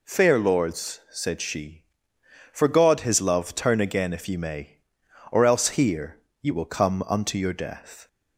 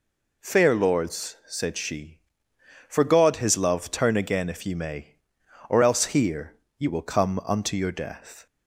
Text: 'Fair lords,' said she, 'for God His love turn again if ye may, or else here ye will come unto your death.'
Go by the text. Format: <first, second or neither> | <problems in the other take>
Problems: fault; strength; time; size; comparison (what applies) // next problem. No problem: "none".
neither | pauses between "here" and "ye"; slight; the same in both